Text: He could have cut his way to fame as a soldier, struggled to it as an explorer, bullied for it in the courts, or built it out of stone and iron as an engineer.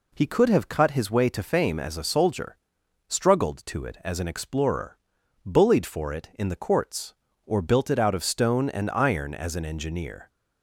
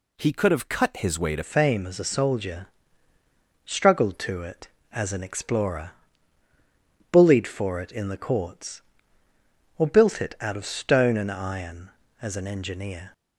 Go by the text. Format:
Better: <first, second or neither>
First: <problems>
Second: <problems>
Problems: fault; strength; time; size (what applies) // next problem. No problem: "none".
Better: first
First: none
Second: changes voice at "fame"; from 1.4 s on; 11.7 s long